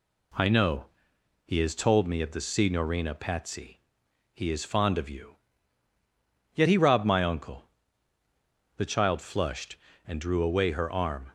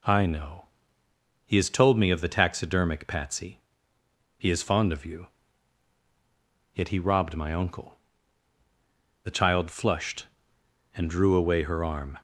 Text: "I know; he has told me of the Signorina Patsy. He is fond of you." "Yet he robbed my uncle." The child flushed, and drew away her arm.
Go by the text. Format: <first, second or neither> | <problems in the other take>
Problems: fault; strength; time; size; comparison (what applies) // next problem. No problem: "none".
first | says "Taxidermic" for "Signorina"; at 2.2 s